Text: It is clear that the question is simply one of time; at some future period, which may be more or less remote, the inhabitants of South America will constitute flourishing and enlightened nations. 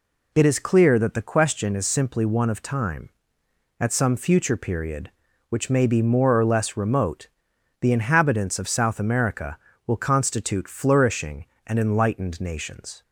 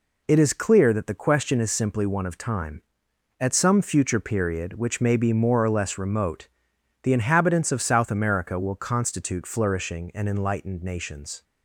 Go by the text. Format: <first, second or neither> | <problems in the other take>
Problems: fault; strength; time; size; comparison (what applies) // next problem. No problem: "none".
neither | none